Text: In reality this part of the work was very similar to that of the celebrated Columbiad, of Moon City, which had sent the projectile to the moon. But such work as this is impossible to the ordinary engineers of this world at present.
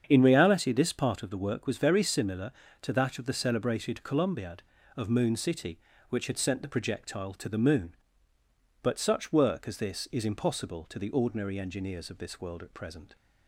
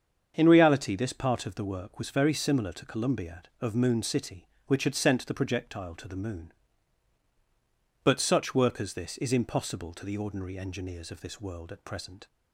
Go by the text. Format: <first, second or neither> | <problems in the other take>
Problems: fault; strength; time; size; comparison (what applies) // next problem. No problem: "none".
first | starts louder than the rest; strong; until 1.3 s; 7 dB; strong in the first // skips "that of the celebrated"; at 2.8 s